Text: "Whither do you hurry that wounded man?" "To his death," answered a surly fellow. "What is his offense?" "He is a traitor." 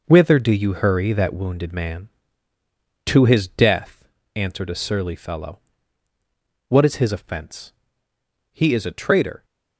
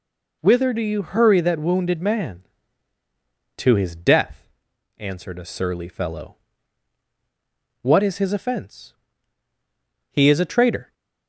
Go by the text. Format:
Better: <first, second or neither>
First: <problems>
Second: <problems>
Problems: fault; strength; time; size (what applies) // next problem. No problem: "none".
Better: second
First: gets quieter; strong; throughout; 9 dB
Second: none